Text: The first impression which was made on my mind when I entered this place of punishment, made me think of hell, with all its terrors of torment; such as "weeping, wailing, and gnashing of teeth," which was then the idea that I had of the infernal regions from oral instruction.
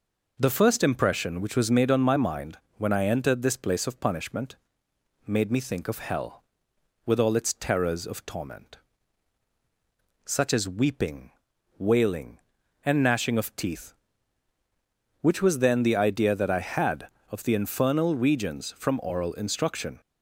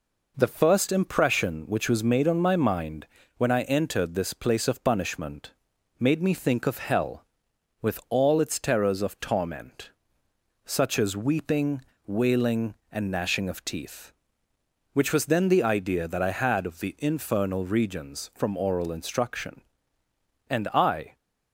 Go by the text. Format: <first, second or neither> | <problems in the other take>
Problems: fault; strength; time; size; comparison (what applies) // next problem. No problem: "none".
first | pauses between "mind" and "when"; slight; at 3.0 s; 0.30 s long; slight in the first // goes on to say "And I"; noticeable; from 20.4 s on; 0.68 s long